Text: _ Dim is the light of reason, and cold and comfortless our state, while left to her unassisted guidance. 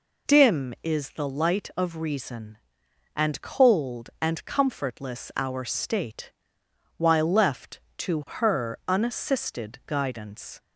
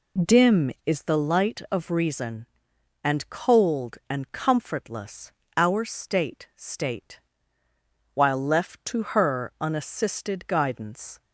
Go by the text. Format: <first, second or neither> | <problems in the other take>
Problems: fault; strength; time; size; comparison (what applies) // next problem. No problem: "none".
first | pauses between "comfortless" and "our"; slight; at 5.3 s; 0.24 s long // says "state" twice; at 6.5 s